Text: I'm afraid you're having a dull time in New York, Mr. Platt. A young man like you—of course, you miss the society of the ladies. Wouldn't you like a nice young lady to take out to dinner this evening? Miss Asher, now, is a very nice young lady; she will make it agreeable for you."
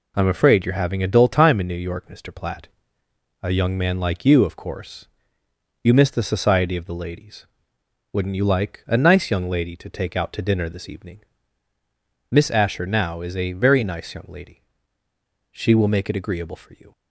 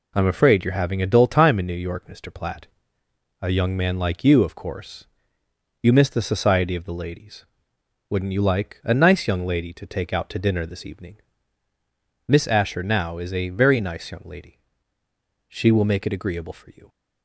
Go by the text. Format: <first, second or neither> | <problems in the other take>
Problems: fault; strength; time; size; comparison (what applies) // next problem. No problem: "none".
neither | none